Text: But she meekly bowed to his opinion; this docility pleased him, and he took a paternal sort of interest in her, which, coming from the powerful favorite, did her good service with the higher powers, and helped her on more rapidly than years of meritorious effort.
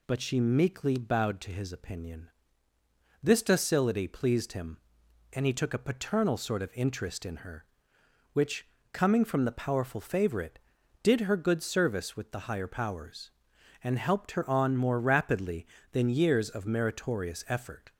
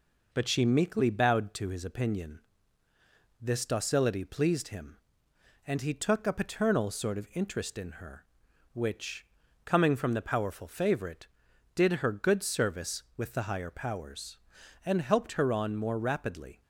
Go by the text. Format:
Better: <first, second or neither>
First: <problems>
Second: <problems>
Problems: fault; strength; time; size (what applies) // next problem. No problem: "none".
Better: first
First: none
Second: stops before "than years of meritorious effort"; at 16.6 s